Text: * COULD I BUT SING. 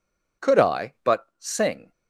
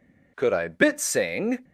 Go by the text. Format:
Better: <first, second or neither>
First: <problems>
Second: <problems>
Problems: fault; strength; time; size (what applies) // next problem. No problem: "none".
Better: first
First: none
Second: says "Bit" for "BUT"; at 0.6 s